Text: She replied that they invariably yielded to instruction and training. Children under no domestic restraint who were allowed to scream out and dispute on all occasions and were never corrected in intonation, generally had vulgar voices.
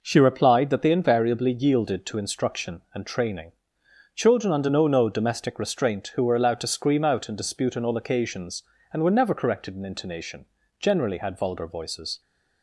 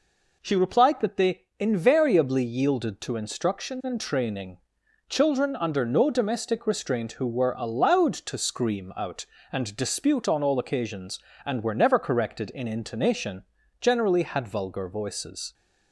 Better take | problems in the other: second | says "no" twice; at 4.8 s

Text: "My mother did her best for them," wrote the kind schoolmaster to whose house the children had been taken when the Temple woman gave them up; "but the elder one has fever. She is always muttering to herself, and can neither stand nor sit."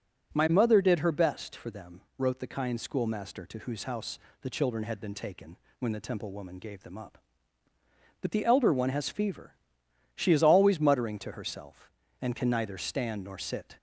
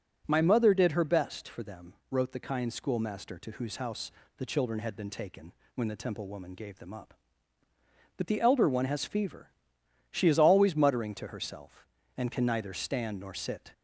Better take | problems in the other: neither | pauses between "house" and "the"; slight; the same in both // pauses between "taken" and "when"; slight; the same in both

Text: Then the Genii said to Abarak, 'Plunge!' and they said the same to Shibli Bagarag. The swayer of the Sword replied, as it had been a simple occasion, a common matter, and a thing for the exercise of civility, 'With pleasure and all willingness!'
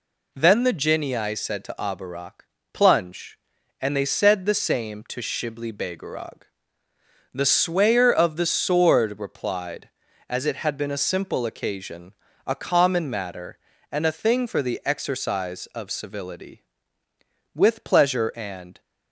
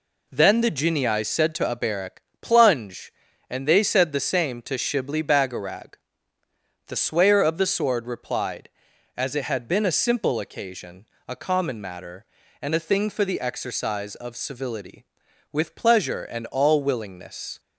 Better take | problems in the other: second | stops before "all willingness"; at 18.7 s

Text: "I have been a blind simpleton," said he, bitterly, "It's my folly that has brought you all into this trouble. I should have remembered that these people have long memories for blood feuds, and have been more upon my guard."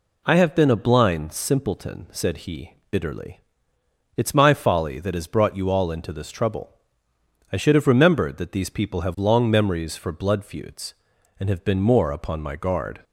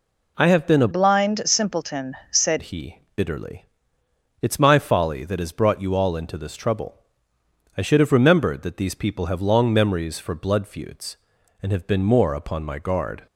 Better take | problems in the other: first | changes voice from "blind" to "said"; from 0.9 to 2.5 s; 1.6 s long

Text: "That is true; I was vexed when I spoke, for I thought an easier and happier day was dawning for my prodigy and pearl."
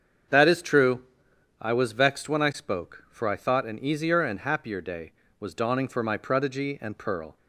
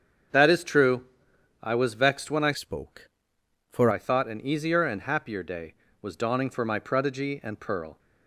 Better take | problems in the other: first | starts louder than the rest; strong; until 1.8 s; 7.5 dB; strong in the first // changes voice from "spoke" to "for"; from 2.5 to 3.8 s; 1.3 s long

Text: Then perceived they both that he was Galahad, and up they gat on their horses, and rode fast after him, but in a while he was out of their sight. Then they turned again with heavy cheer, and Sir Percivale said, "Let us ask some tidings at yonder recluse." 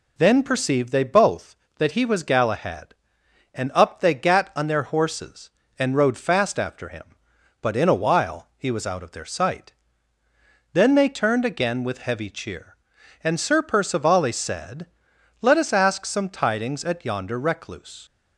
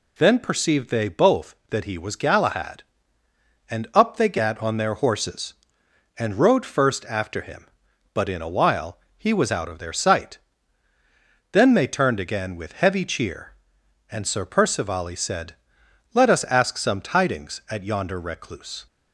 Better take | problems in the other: first | says "first" for "fast"; at 6.6 s // pauses between "while" and "he"; slight; at 8.9 s; 0.18 s long

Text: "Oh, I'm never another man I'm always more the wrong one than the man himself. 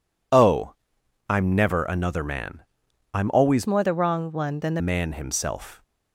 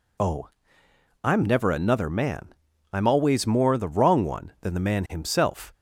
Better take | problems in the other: second | pauses between "man" and "I'm"; noticeable; at 2.6 s; 0.52 s long; also in the second // changes voice from "more" to "the"; from 3.6 to 4.8 s; 1.2 s long

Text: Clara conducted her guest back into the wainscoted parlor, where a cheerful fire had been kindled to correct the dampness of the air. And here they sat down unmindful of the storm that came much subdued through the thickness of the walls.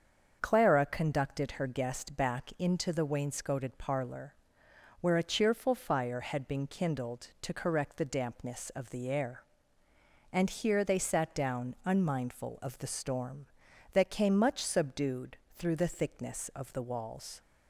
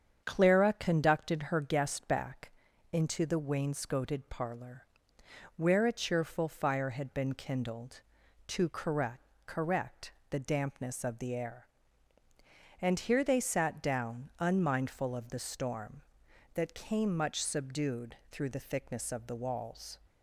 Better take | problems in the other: first | starts louder than the rest; strong; until 1.2 s; 8 dB; also in the first // pauses between "back" and "into"; at 2.5 s; 0.40 s long // says "correct" twice; at 9.4 s // pauses between "subdued" and "through"; slight; at 18.1 s; 0.16 s long; slight in the first

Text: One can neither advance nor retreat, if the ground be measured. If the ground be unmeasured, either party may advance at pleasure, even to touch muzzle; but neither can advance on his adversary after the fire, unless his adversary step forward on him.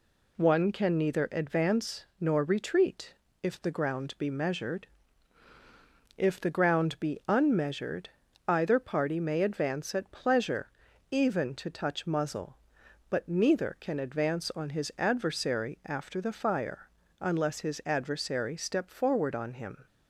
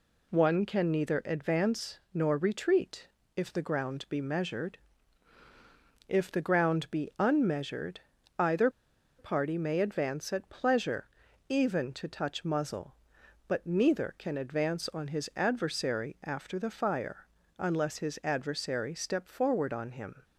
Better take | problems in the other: first | pauses between "either" and "party"; noticeable; at 8.6 s; 0.49 s long

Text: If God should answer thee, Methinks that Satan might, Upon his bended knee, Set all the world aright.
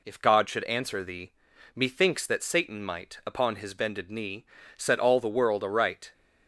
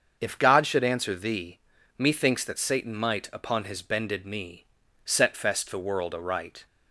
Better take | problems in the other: first | starts louder than the rest; until 1.2 s; 7 dB // says "fest" for "all"; at 5.3 s

